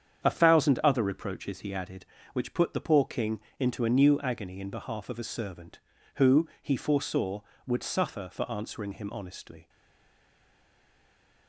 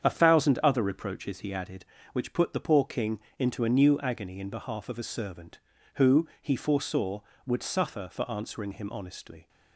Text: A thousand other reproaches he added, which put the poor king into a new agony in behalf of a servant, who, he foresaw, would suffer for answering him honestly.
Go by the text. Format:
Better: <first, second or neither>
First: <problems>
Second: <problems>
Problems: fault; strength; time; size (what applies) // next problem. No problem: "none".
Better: second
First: starts louder than the rest; strong; until 1.2 s; 8 dB // pauses between "king" and "into"; slight; at 3.4 s; 0.18 s long // stays silent after the last word; noticeable; from 9.6 s on; 1.8 s long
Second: starts louder than the rest; strong; until 1.0 s; 8 dB // pauses between "king" and "into"; slight; at 3.2 s; 0.18 s long